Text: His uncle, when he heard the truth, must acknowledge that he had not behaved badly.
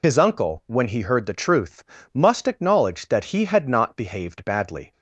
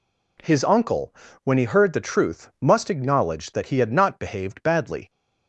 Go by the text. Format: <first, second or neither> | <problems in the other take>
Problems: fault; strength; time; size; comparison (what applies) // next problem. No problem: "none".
second | loses the start of "His"; at 0.0 s; 30 ms